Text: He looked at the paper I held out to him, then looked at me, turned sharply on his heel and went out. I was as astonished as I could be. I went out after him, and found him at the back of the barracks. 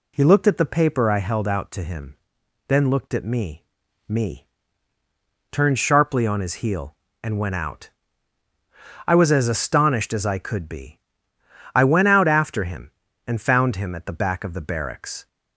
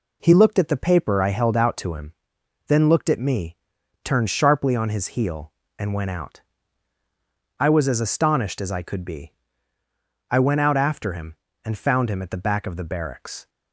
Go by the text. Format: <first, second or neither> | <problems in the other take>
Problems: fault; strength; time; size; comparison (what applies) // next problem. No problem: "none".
second | says "me" twice; at 4.0 s